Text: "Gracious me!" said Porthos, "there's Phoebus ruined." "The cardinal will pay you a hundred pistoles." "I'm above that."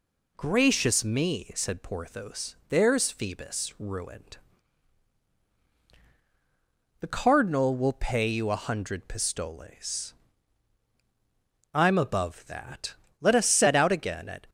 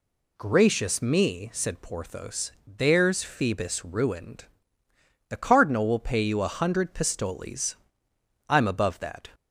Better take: second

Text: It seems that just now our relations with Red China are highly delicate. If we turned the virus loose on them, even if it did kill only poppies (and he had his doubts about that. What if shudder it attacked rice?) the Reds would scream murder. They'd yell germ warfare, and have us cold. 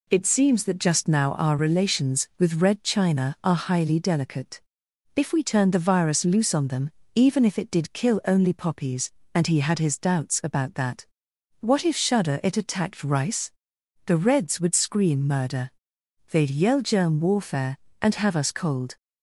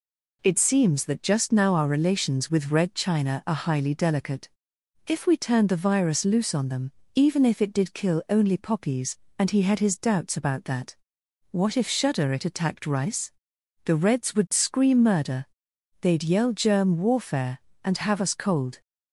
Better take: neither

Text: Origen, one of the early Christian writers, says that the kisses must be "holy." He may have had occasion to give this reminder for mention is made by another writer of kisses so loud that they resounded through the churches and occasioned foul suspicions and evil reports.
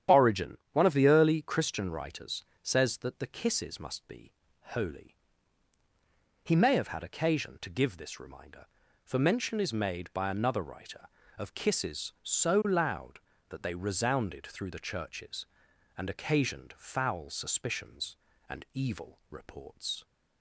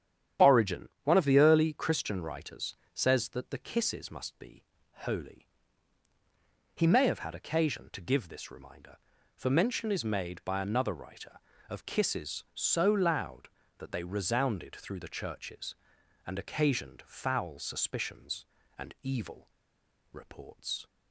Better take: first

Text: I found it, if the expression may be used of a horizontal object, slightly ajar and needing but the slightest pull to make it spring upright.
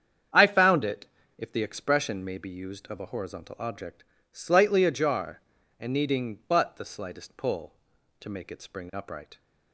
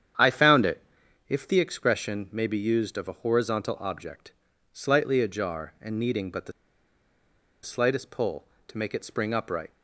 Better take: first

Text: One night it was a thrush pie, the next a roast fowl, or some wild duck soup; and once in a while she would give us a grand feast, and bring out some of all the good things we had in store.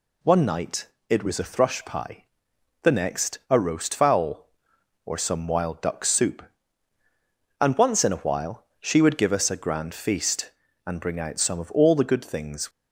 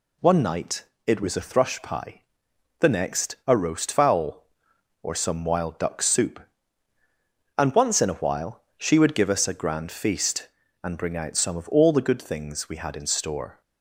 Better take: second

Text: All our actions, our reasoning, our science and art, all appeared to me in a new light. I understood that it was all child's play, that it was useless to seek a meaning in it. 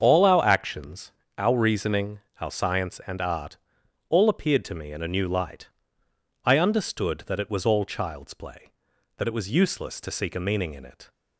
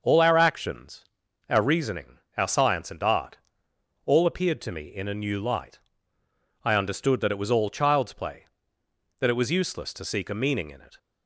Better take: neither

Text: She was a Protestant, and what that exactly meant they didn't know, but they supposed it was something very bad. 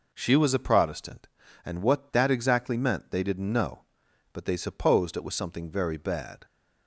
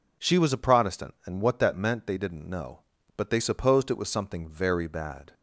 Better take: first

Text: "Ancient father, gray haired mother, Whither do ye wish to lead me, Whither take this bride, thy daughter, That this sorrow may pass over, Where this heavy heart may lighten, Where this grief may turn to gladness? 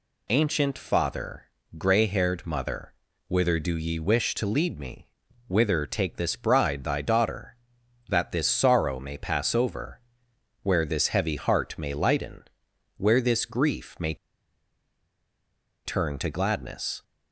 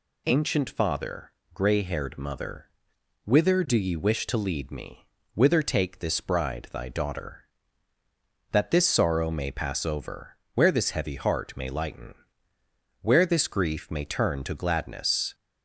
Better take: second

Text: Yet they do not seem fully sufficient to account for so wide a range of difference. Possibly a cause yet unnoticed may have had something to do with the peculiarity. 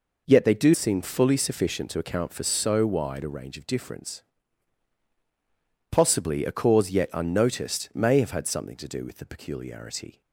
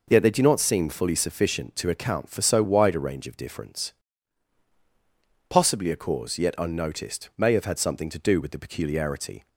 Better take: second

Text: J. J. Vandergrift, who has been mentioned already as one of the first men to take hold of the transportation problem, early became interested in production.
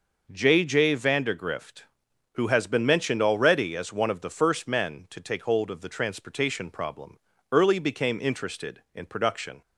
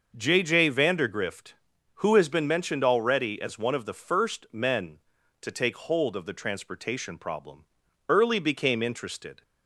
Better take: first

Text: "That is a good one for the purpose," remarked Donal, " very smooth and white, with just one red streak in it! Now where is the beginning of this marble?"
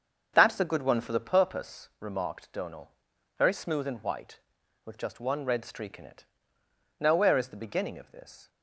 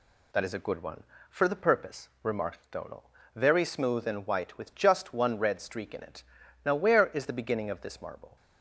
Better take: second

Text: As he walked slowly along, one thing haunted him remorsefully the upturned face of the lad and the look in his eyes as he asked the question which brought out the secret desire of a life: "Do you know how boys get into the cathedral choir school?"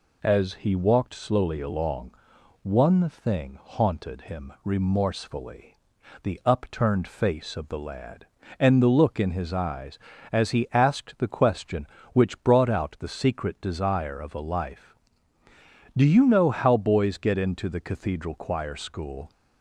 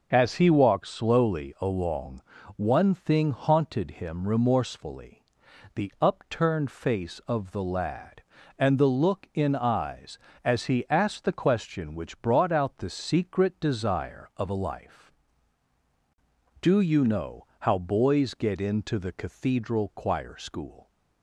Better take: first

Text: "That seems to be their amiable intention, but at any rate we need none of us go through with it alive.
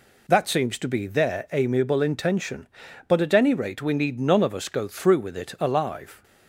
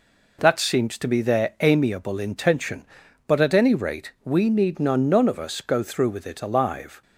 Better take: first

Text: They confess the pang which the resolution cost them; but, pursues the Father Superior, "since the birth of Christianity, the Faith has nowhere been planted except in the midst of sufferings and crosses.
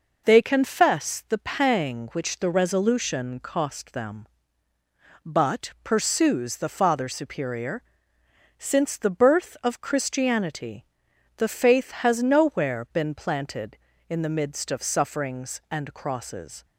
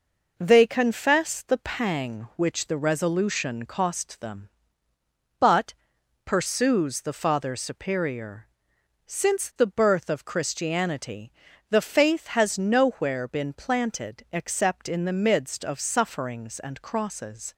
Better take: second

